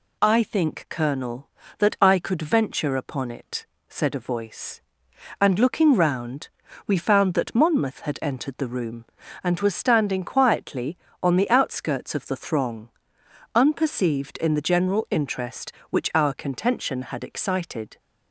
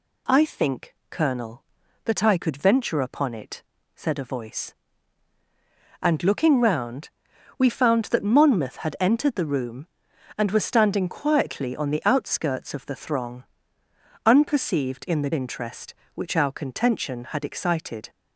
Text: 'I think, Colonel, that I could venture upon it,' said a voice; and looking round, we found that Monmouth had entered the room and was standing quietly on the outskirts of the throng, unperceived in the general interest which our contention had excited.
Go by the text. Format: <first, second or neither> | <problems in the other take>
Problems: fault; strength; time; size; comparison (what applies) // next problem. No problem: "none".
first | skips "general"; at 15.3 s